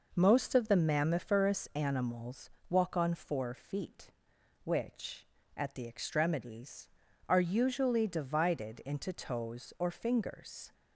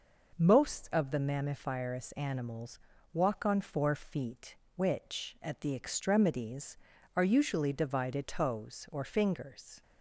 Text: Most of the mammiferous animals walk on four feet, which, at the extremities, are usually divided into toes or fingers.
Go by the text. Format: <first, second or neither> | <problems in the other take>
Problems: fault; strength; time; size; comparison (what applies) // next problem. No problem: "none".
first | pauses between "animals" and "walk"; slight; at 2.7 s; 0.32 s long; slight in the first // skips "into"; at 8.2 s